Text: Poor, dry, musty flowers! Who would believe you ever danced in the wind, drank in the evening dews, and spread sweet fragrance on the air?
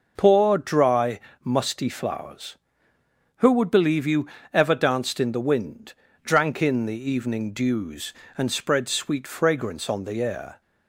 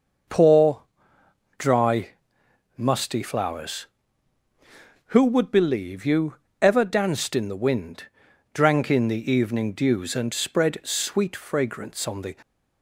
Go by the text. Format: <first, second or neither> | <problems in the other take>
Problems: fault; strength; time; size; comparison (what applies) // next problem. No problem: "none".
first | pauses between "you" and "ever"; slight; at 6.3 s; 0.26 s long; slight in the first // stops before "air"; at 12.4 s